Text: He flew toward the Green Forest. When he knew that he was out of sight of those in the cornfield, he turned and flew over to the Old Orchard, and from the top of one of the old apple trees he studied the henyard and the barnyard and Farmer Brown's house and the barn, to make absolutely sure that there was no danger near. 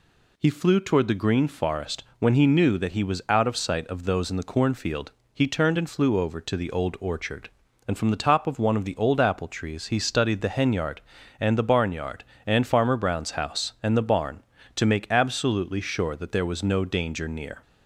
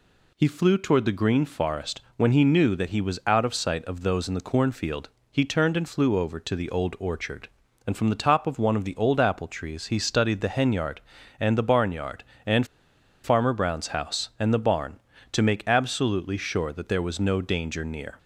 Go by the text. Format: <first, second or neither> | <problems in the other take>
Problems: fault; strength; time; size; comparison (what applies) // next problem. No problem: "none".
first | pauses between "and" and "Farmer"; noticeable; at 12.6 s; 0.58 s long